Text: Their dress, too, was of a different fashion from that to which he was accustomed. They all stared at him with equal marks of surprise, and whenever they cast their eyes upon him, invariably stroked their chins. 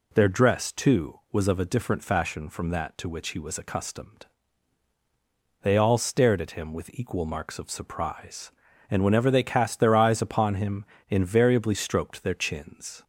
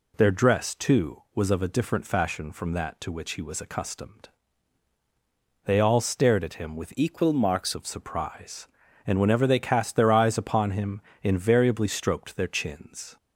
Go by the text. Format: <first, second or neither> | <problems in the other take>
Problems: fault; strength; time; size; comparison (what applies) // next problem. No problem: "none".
first | changes voice from "equal" to "marks"; from 6.9 to 7.7 s; 0.8 s long